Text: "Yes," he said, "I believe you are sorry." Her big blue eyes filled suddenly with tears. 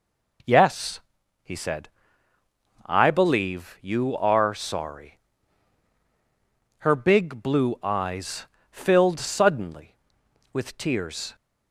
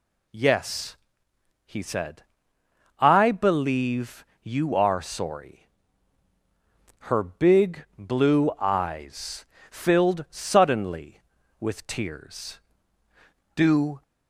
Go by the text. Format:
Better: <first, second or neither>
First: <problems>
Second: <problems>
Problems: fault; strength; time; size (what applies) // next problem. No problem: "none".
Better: first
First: pauses between "eyes" and "filled"; slight; at 8.4 s; 0.24 s long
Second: pauses between "believe" and "you"; slight; at 4.2 s; 0.16 s long // pauses between "eyes" and "filled"; slight; at 9.4 s; 0.24 s long // goes on to say "Do"; slight; from 13.5 s on; 0.46 s long